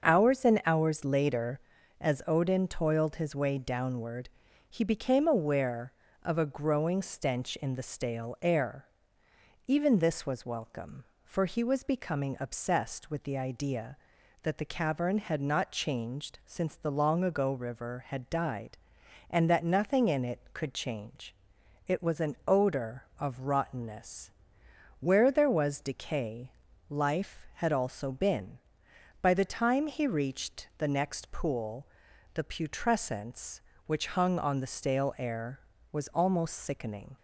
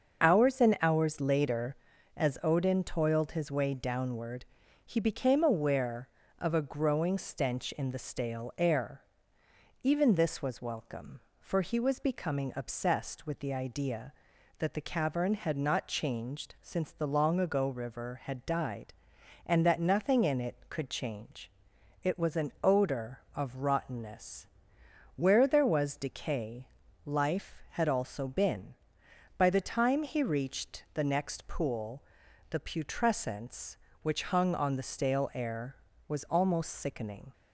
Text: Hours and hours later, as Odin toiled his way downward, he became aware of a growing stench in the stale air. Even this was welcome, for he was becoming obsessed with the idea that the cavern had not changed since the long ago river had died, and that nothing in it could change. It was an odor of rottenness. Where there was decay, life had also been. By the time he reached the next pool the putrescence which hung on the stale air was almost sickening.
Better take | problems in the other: first | loses the start of "Hours"; at 0.2 s; 20 ms // starts louder than the rest; until 1.2 s; 6.5 dB; also in the first // pauses between "pool" and "the"; noticeable; at 32.0 s; 0.48 s long; noticeable in the first

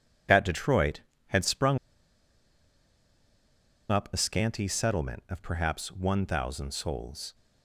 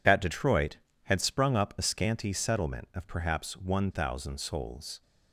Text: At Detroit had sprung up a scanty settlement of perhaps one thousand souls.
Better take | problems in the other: second | pauses between "sprung" and "up"; strong; at 1.7 s; 2.1 s long

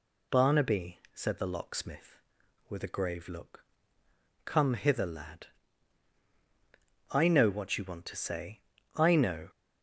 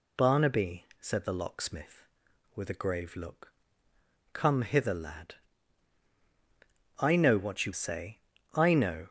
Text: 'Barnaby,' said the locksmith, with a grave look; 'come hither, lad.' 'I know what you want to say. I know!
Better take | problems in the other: first | skips "want to"; at 7.7 s

